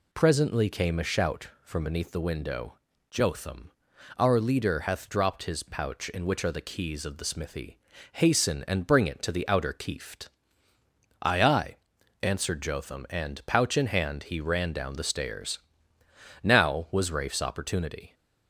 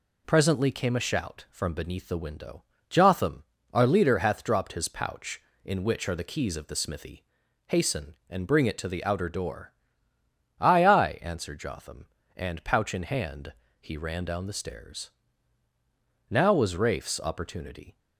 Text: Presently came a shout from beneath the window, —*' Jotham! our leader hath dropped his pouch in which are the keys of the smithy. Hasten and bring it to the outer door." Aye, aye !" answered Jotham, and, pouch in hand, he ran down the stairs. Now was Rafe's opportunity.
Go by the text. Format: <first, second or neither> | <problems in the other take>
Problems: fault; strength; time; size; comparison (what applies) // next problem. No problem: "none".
second | says "keeft" for "door"; at 9.7 s